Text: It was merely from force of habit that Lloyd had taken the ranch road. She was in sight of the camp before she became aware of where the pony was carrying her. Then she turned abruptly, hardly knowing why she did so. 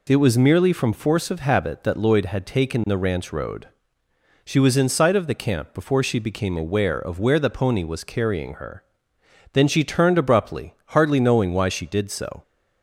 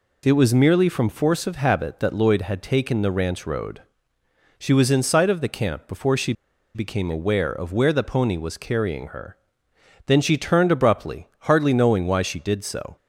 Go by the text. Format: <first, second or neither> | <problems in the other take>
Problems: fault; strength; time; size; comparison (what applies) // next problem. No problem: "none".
first | pauses between "she" and "became"; at 6.3 s; 0.42 s long